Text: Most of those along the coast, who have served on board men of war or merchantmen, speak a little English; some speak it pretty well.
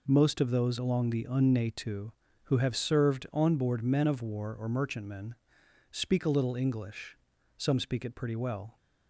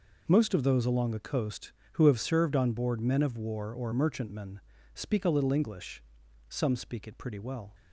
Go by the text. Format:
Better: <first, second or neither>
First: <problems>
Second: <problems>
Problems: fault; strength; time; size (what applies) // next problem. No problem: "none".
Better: second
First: says "unnatu" for "coast"; at 1.2 s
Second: none